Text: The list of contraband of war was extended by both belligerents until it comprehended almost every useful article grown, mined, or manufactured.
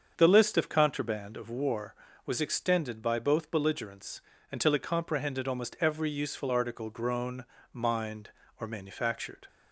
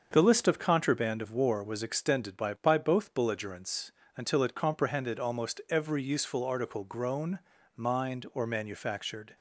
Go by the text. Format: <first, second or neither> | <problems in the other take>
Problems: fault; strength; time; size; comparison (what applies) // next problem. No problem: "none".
first | starts louder than the rest; until 1.1 s; 6.5 dB; also in the first // says "by" twice; at 2.5 s // pauses between "belligerents" and "until"; slight; at 3.9 s; 0.26 s long; slight in the first